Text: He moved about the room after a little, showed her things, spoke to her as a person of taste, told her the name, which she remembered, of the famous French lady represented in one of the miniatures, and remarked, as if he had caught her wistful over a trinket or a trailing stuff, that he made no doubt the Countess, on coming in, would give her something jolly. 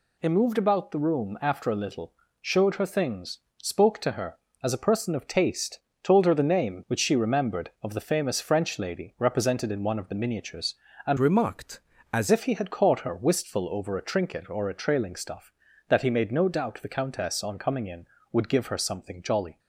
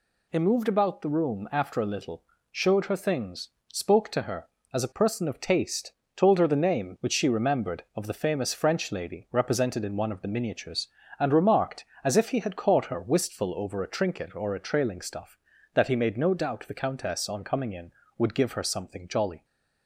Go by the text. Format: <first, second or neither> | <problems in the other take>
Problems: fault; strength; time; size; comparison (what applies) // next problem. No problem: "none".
second | changes voice from "remarked" to "as"; from 11.1 to 12.2 s; 1.1 s long